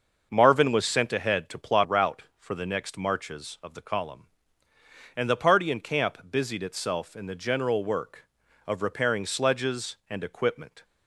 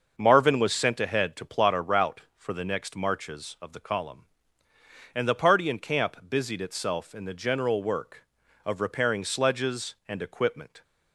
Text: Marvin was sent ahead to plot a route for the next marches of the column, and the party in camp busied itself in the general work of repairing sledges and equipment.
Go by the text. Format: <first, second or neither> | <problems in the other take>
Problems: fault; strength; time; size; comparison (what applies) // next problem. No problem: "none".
second | starts louder than the rest; noticeable; until 1.3 s; 6 dB; also in the second // skips "a"; at 1.8 s